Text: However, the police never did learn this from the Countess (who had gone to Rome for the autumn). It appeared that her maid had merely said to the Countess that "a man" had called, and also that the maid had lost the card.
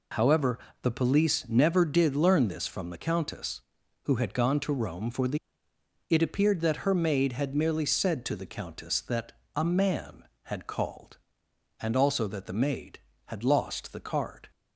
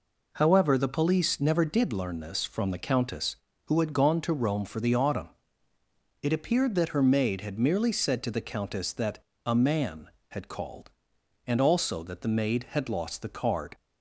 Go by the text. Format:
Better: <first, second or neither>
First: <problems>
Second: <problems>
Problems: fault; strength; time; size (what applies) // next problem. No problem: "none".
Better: second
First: skips "autumn"; at 5.7 s // pauses between "that" and "a"; slight; at 9.3 s; 0.24 s long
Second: pauses between "that" and "a"; slight; at 9.2 s; 0.22 s long